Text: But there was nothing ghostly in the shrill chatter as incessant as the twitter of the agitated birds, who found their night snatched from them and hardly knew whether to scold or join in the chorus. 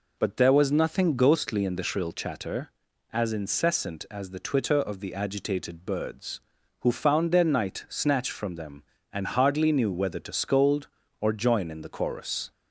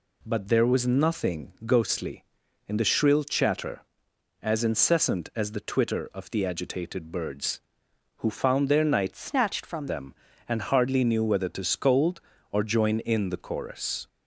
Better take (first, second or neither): first